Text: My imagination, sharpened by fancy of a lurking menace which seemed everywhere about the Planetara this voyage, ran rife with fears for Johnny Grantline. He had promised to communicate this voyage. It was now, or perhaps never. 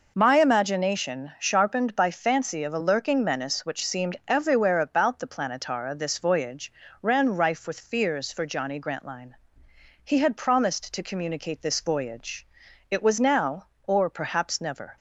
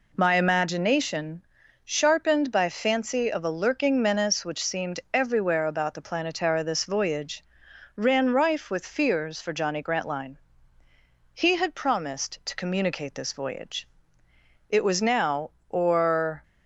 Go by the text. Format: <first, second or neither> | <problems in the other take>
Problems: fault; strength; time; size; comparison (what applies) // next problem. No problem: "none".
first | stops before "perhaps never"; at 16.4 s